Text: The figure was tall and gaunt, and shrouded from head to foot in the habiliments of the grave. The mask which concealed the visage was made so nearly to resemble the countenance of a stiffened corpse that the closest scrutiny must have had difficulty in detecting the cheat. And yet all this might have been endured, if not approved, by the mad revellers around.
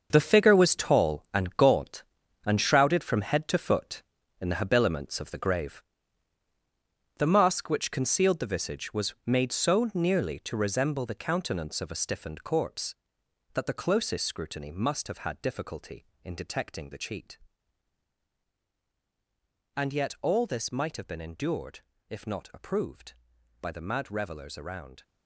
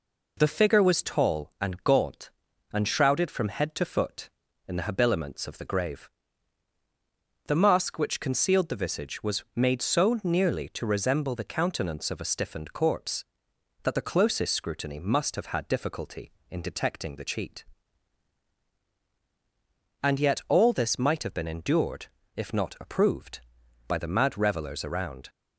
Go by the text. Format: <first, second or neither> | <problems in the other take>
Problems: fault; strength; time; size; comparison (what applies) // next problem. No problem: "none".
second | gets quieter; strong; throughout; 11.5 dB